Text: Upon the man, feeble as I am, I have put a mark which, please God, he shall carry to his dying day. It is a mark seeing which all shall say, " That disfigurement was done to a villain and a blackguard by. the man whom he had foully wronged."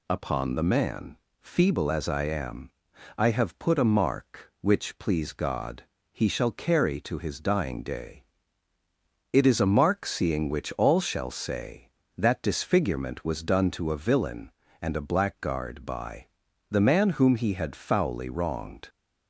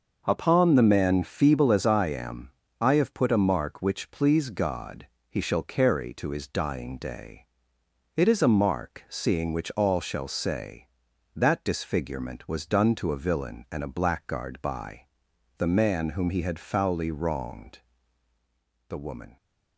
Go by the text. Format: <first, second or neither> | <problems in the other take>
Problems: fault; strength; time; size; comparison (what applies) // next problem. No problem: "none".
first | starts louder than the rest; noticeable; until 1.2 s; 6 dB // goes on to say "The woman"; slight; from 18.8 s on; 0.48 s long